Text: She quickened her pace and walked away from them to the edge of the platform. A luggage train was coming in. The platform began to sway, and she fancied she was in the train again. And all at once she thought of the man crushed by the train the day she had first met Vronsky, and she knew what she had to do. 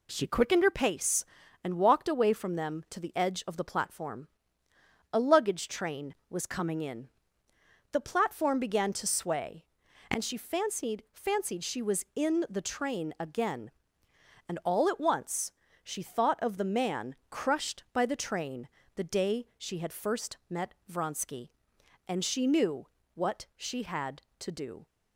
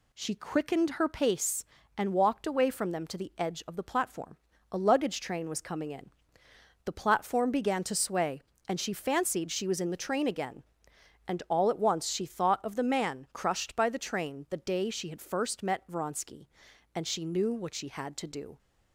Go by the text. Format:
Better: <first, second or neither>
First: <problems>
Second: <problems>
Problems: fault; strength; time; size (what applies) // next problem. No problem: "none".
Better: second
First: says "fancied" twice; at 11.1 s // pauses between "once" and "she"; slight; at 15.5 s; 0.32 s long // pauses between "man" and "crushed"; slight; at 17.1 s; 0.16 s long // pauses between "train" and "the"; slight; at 18.6 s; 0.28 s long // pauses between "met" and "Vronsky"; slight; at 20.7 s; 0.16 s long // pauses between "knew" and "what"; slight; at 22.8 s; 0.26 s long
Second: none